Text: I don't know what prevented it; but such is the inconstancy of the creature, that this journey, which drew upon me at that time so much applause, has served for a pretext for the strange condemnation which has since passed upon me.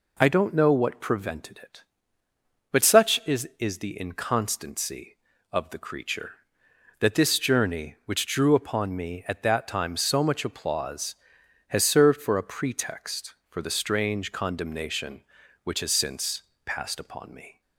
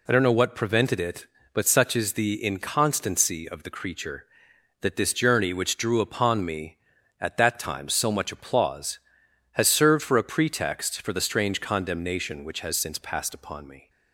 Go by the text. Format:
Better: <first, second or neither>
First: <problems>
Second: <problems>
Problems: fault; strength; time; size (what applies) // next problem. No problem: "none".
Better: second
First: says "is" twice; at 3.5 s // pauses between "since" and "passed"; slight; at 16.4 s; 0.24 s long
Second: none